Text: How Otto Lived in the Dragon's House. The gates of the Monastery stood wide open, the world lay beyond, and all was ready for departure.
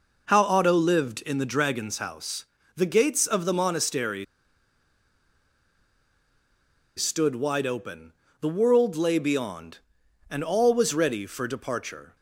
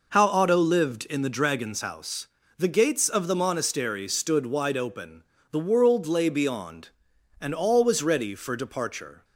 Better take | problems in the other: second | pauses between "Monastery" and "stood"; strong; at 4.2 s; 2.7 s long

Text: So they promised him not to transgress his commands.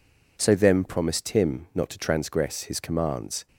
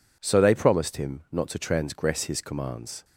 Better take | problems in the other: second | says "them" for "they"; at 0.5 s

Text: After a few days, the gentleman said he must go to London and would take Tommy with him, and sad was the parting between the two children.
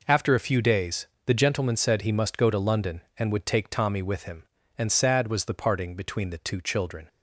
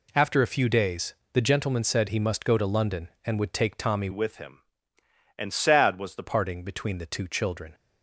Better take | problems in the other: first | changes voice from "with" to "the"; from 4.1 to 6.2 s; 2.1 s long

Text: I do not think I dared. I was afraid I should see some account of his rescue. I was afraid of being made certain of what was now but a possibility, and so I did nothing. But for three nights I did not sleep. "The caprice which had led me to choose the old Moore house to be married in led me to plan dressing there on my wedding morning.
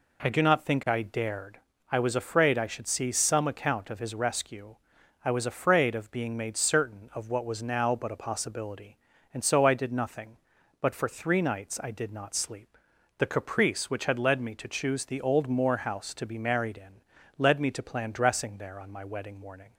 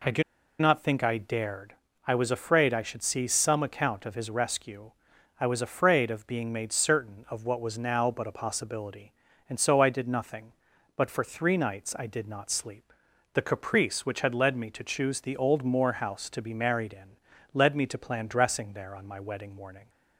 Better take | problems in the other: first | pauses between "do" and "not"; at 0.2 s; 0.38 s long // pauses between "in" and "led"; slight; at 17.1 s; 0.36 s long; slight in the first

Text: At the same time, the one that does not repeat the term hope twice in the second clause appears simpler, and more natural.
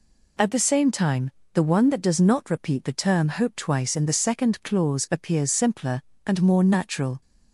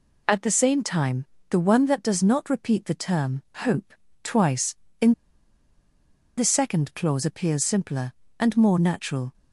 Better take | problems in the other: first | pauses between "hope" and "twice"; slight; at 3.9 s; 0.32 s long // pauses between "in" and "the"; strong; at 5.1 s; 1.2 s long

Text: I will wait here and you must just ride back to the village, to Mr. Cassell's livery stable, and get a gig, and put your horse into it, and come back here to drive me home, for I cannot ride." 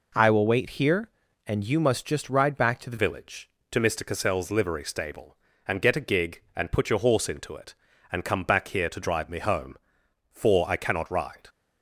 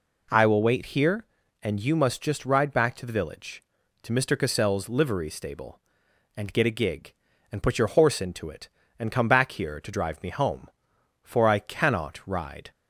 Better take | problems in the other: second | changes voice at "village"; from 2.9 s on; 8.5 s long

